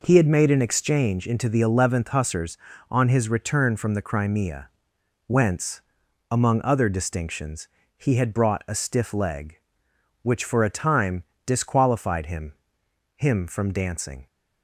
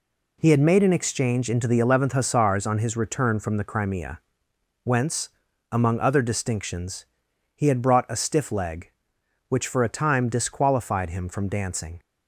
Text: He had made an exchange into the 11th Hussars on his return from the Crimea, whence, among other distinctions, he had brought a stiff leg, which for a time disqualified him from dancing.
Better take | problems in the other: second | pauses between "time" and "disqualified"; slight; at 11.2 s; 0.24 s long // says "him" twice; at 13.1 s

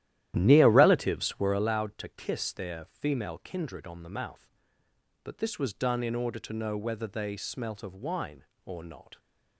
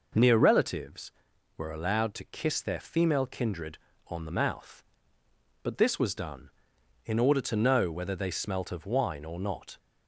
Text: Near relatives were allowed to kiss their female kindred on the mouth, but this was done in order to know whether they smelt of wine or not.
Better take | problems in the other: second | starts louder than the rest; strong; until 1.8 s; 12.5 dB

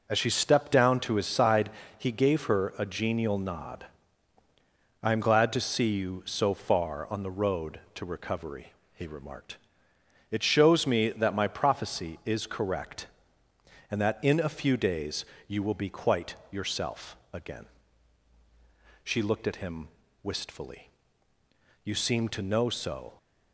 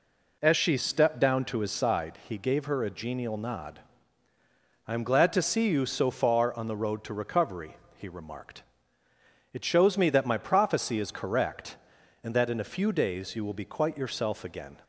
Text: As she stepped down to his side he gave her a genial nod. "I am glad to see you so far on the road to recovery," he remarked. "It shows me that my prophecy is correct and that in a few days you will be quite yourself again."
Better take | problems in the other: second | pauses between "side" and "he"; slight; at 1.6 s; 0.28 s long // pauses between "days" and "you"; slight; at 15.2 s; 0.20 s long // pauses between "quite" and "yourself"; slight; at 16.3 s; 0.16 s long // pauses between "yourself" and "again"; slight; at 17.1 s; 0.16 s long // goes on to say "She looked at him wistfully You seem to know so"; strong; from 19.0 s on; 4.1 s long

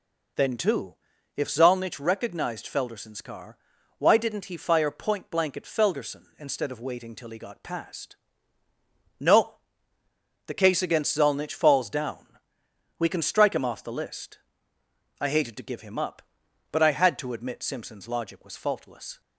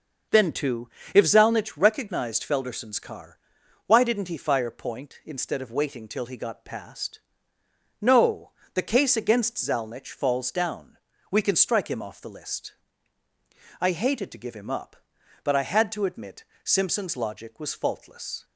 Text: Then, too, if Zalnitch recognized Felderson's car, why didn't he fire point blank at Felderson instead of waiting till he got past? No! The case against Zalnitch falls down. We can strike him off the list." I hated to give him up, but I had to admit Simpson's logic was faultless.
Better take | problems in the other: first | starts louder than the rest; until 1.5 s; 6.5 dB // skips "blank at Felderson"; at 5.2 s // pauses between "admit" and "Simpson's"; slight; at 16.4 s; 0.22 s long

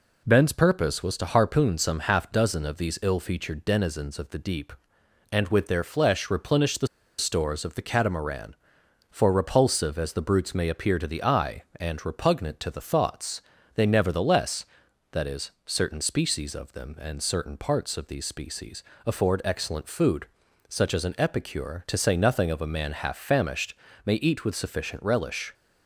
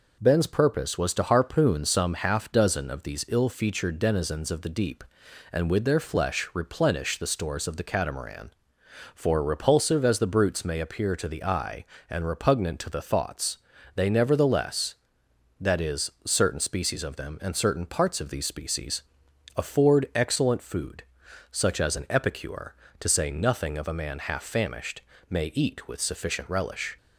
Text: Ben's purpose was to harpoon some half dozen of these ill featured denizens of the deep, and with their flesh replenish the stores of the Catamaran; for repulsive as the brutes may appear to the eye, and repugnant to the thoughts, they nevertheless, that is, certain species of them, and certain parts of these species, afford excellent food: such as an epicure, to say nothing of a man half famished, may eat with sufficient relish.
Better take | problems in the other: second | pauses between "the" and "stores"; slight; at 6.8 s; 0.31 s long

